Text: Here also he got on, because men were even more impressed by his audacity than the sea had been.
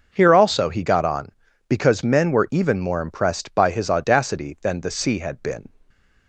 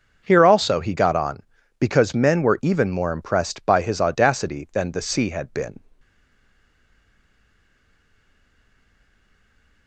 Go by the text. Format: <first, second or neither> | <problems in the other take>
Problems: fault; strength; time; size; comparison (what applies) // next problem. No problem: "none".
first | stays silent after the last word; strong; from 6.0 s on; 3.8 s long